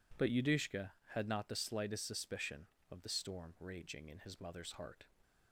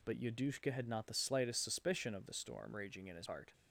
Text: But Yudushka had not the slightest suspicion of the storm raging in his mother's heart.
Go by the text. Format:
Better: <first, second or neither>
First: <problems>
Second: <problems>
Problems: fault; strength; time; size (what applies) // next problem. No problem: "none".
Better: first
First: none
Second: skips "mother's"; at 3.2 s